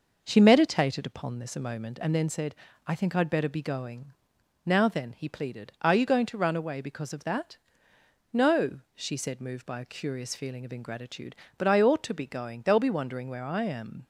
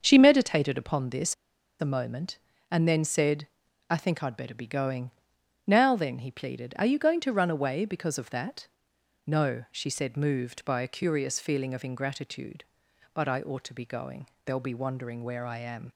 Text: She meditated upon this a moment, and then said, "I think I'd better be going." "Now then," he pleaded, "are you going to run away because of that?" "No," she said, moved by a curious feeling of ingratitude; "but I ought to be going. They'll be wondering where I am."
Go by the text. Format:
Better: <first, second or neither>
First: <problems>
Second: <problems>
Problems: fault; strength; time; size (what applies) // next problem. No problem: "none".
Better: first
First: none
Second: starts louder than the rest; until 1.0 s; 7 dB // pauses between "this" and "a"; at 1.3 s; 0.45 s long